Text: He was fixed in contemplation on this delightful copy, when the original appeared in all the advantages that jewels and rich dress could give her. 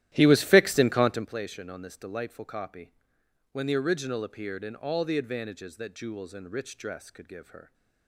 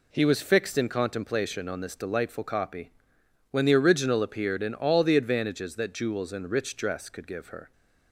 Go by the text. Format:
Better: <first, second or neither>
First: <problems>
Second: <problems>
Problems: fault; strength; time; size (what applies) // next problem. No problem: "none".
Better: second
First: starts louder than the rest; strong; until 1.4 s; 13.5 dB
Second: none